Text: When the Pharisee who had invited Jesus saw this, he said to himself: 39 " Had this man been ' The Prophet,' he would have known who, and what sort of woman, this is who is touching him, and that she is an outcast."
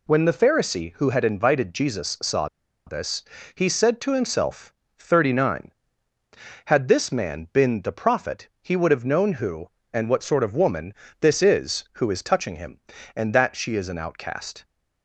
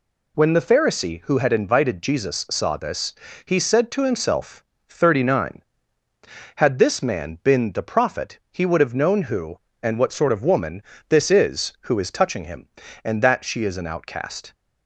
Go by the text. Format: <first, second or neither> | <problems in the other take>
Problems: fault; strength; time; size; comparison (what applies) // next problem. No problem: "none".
second | pauses between "saw" and "this"; at 2.4 s; 0.40 s long